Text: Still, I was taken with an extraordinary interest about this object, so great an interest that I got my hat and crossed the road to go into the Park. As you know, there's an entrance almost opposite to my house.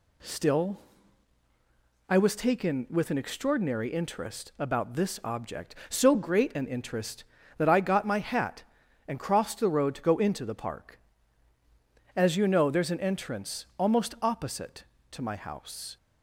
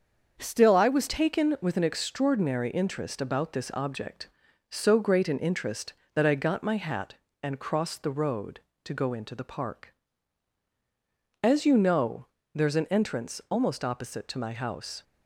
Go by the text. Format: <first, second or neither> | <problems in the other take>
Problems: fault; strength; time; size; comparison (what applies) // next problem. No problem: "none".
first | starts louder than the rest; until 1.4 s; 7 dB // changes voice at "taken"; from 1.0 s on; 14.0 s long